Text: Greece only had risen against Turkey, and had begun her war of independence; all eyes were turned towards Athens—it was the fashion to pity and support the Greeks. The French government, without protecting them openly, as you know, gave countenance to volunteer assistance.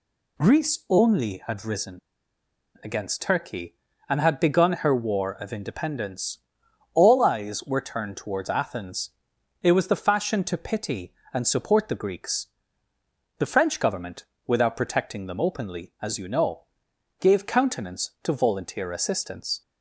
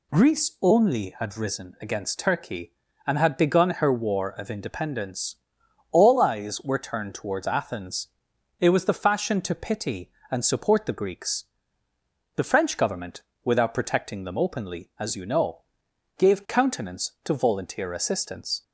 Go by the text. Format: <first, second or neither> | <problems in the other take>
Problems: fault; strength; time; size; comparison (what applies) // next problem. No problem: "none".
second | pauses between "risen" and "against"; noticeable; at 1.9 s; 0.83 s long